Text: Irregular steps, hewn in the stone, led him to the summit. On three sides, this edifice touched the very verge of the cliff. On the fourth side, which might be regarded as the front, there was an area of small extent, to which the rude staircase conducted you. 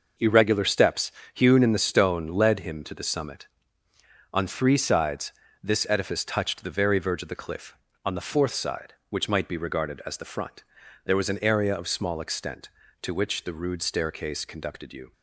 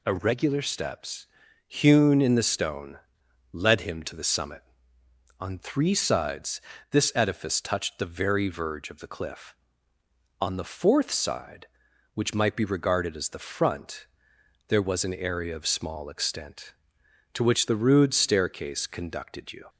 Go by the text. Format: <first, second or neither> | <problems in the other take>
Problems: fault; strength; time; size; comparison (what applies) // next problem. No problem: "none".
neither | none